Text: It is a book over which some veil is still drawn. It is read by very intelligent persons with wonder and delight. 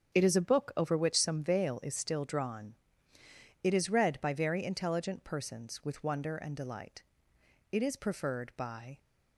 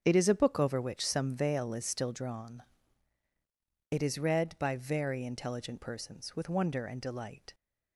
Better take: second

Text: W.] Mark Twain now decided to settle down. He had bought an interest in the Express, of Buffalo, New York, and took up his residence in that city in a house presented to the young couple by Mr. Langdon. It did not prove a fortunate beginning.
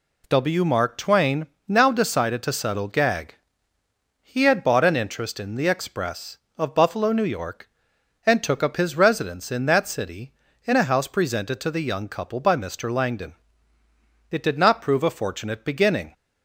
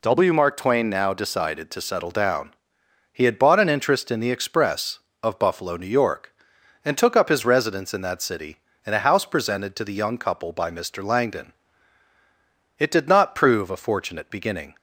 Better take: second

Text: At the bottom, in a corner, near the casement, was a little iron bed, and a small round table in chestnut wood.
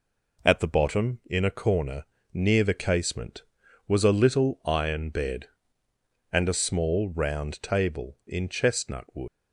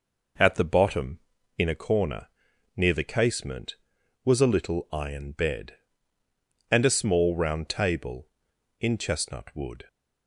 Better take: second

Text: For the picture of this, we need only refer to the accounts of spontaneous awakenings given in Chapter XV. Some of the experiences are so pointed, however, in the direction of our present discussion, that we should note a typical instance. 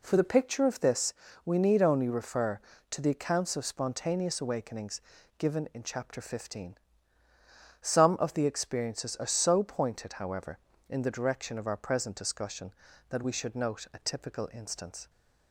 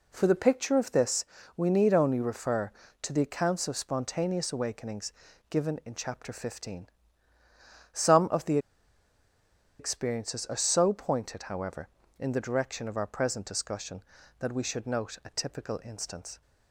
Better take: first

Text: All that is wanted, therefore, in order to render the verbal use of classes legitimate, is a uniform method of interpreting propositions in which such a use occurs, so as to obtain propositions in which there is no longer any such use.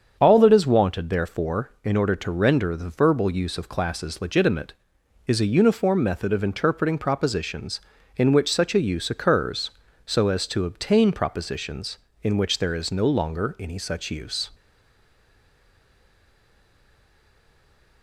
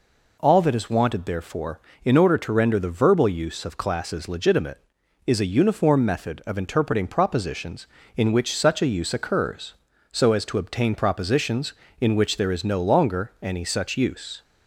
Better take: second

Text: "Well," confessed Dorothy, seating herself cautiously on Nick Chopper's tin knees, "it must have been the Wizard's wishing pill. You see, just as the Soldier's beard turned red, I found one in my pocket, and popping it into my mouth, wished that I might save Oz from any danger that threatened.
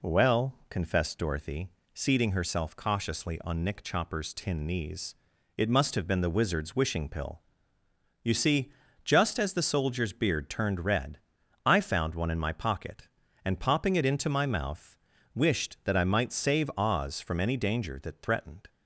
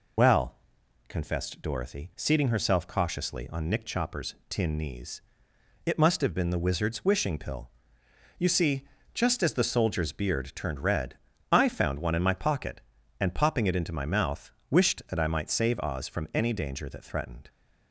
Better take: first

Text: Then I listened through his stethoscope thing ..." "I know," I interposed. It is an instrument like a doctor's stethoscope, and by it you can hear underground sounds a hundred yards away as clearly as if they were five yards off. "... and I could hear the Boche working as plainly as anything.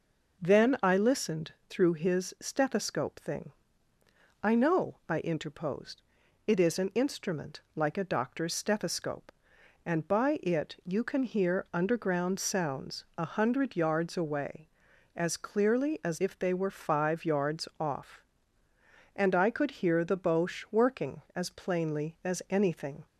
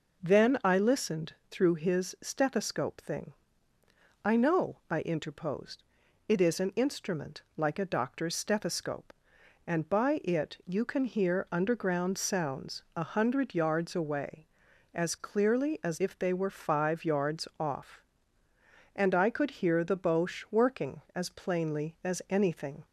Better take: neither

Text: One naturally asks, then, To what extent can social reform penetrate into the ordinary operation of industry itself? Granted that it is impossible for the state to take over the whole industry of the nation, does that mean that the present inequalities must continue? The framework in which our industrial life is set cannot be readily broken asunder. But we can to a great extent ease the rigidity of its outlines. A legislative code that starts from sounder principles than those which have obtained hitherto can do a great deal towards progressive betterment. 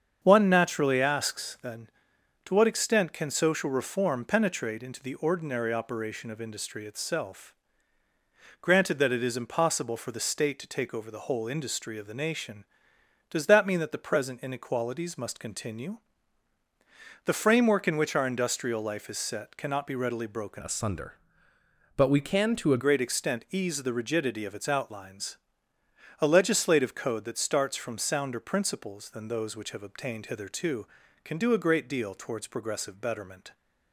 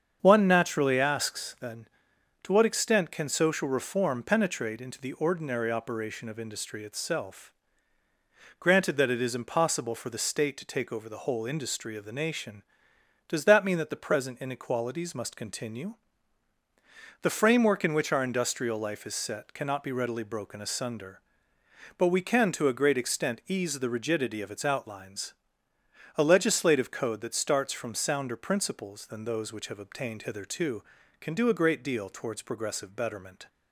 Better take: second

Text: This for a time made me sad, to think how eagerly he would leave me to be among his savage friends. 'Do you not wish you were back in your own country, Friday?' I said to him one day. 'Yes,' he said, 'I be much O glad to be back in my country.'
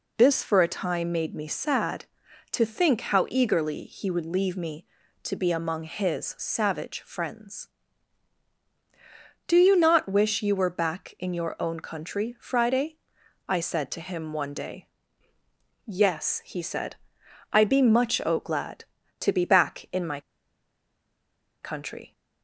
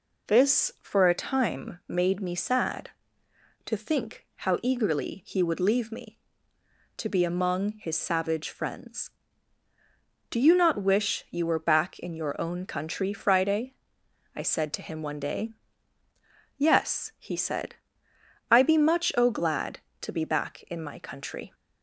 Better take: second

